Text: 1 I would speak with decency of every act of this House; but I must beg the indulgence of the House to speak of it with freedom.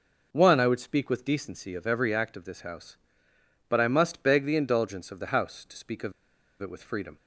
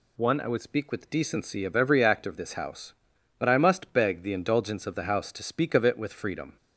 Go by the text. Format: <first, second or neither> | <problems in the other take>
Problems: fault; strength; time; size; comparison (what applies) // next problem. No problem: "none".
second | pauses between "of" and "it"; noticeable; at 6.1 s; 0.47 s long